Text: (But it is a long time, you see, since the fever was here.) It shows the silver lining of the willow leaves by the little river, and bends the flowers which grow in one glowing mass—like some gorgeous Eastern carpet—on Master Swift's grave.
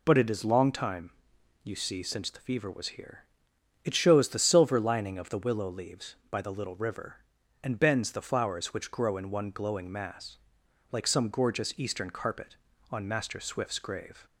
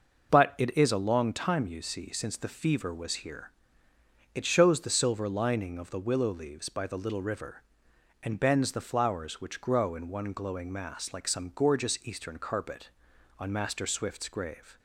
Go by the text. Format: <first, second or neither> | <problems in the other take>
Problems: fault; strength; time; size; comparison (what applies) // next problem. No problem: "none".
second | skips "a"; at 0.4 s